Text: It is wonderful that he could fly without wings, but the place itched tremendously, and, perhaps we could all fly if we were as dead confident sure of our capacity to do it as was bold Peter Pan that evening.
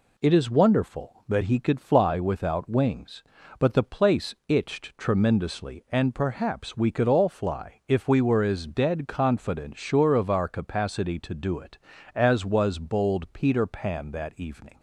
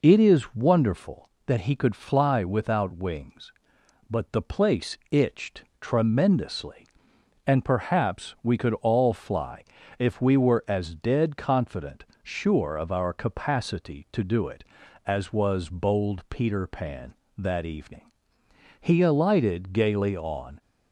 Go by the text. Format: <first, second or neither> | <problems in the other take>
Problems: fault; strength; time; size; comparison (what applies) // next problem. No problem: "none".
first | pauses between "itched" and "tremendously"; slight; at 5.6 s; 0.18 s long // pauses between "fly" and "if"; slight; at 9.6 s; 0.34 s long // pauses between "confident" and "sure"; slight; at 12.0 s; 0.18 s long // goes on to say "He alighted gaily on"; strong; from 18.8 s on; 1.8 s long